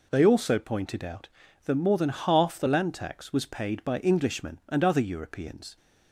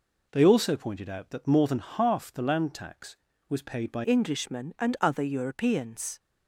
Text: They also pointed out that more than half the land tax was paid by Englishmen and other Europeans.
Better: first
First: none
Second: changes voice at "Englishmen"; from 4.0 s on; 2.1 s long

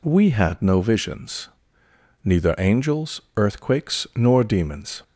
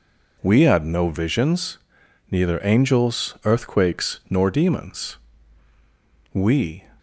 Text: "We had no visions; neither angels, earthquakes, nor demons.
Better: first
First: none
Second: goes on to say "We"; from 6.3 s on; 0.52 s long

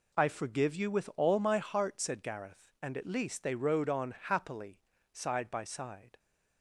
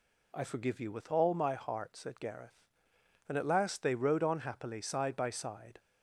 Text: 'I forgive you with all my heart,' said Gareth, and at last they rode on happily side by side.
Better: second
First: says "least" for "last"; at 3.0 s // pauses between "happily" and "side"; slight; at 4.7 s; 0.32 s long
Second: none

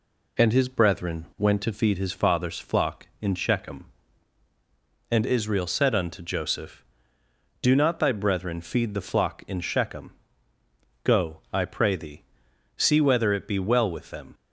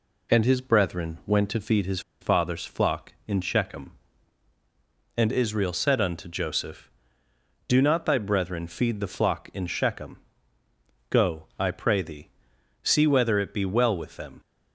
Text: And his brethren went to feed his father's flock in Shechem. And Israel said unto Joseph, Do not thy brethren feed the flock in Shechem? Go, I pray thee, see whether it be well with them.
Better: first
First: none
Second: pauses between "his" and "father's"; slight; at 1.9 s; 0.21 s long

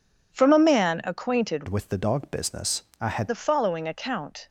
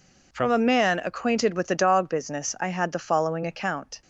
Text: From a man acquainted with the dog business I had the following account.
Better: second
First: changes voice from "with" to "had"; from 1.6 to 3.2 s; 1.6 s long // pauses between "business" and "I"; slight; at 2.8 s; 0.18 s long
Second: none

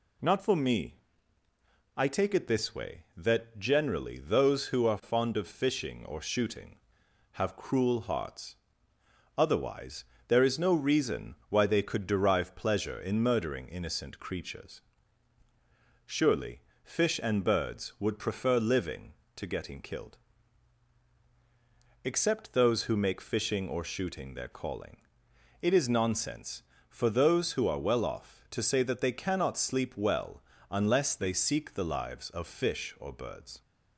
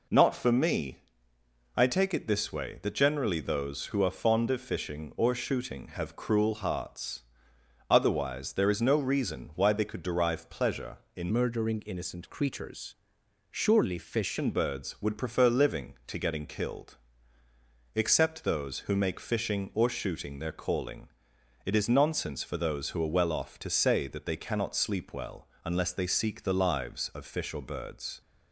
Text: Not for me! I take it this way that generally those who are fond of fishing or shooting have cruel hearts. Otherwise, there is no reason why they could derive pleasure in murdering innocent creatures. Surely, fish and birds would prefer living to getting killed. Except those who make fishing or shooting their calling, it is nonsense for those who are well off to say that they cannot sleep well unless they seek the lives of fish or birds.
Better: first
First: pauses between "well" and "unless"; slight; at 30.4 s; 0.28 s long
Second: changes voice from "murdering" to "fish"; from 11.3 to 14.3 s; 3.0 s long // pauses between "well" and "unless"; slight; at 25.4 s; 0.18 s long

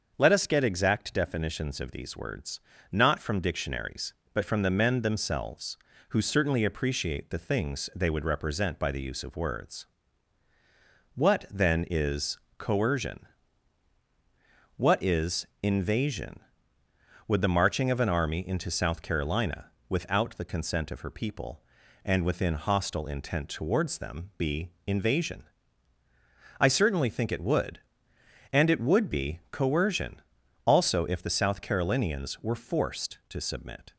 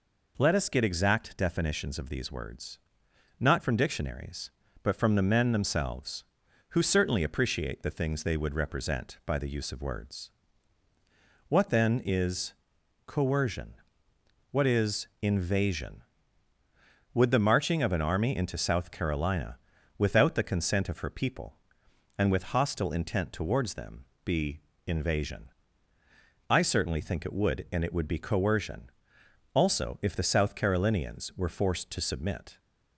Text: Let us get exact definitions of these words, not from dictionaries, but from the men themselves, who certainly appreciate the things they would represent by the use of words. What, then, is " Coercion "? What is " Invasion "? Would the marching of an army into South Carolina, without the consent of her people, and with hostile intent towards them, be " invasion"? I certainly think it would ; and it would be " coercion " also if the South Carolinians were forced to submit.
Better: second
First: starts louder than the rest; until 1.1 s; 6.5 dB // says "within" for "with"; at 22.2 s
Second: none

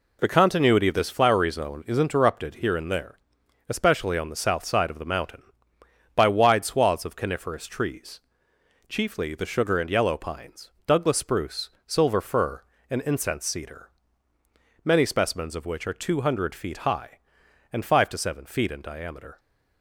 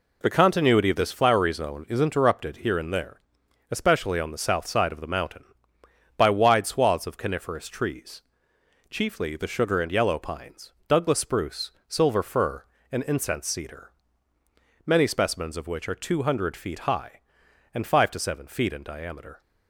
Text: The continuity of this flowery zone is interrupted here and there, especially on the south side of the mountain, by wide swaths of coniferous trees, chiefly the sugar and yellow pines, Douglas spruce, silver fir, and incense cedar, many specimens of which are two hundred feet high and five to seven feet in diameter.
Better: neither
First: none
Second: none

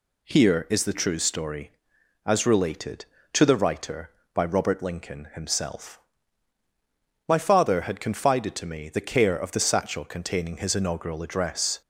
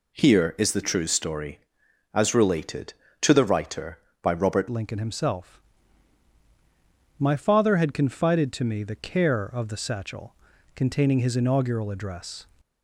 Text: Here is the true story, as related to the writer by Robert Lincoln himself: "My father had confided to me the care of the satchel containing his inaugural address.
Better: first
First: none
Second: changes voice at "Lincoln"; from 4.6 s on; 7.8 s long // pauses between "satchel" and "containing"; at 10.3 s; 0.40 s long

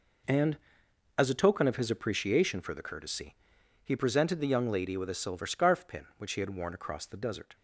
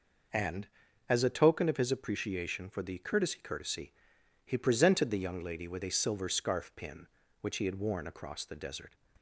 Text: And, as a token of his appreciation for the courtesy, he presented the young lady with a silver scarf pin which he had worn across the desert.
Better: first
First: none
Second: says "courtesy" twice; at 3.4 s

